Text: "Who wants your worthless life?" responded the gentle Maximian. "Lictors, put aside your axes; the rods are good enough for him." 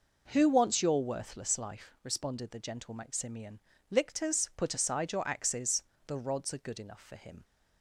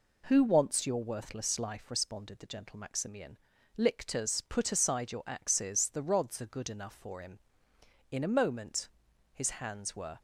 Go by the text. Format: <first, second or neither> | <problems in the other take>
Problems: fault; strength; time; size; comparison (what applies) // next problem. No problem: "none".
first | goes on to say "In a moment his hands were"; strong; from 8.1 s on; 2.1 s long